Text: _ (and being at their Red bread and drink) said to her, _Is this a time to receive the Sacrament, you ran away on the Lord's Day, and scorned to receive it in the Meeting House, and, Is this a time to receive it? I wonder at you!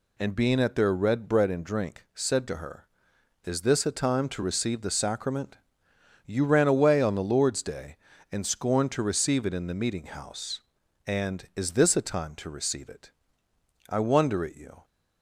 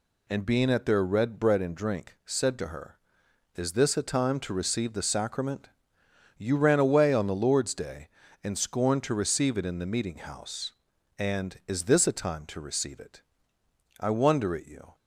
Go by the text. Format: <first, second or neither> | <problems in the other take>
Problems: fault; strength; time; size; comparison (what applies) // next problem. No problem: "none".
neither | none